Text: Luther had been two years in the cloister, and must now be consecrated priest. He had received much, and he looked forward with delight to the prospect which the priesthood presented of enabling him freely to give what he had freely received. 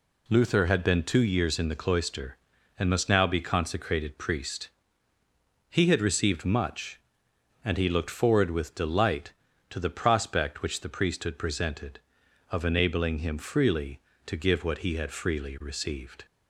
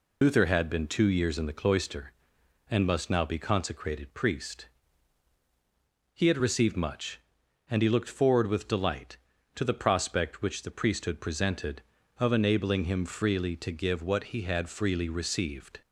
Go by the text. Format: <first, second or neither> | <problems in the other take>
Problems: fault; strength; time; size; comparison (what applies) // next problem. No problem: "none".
first | loses the start of "Luther"; at 0.2 s; 65 ms